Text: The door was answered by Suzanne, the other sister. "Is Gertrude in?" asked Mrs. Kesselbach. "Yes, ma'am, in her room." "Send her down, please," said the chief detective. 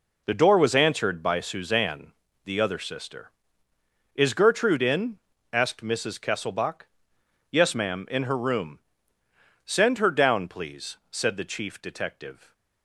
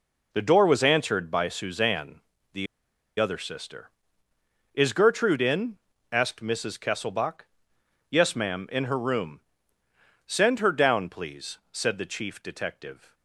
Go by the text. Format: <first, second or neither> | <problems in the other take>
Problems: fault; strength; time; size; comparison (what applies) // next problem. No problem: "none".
first | pauses between "the" and "other"; noticeable; at 2.6 s; 0.53 s long